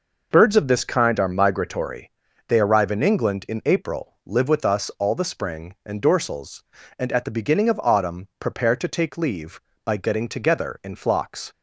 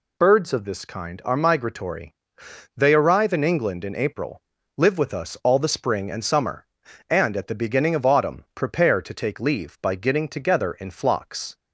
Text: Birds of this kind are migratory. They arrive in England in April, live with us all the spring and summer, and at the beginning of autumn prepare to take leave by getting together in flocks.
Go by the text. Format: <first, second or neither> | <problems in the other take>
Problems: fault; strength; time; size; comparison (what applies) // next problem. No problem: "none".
second | says "dorsals" for "summer"; at 6.0 s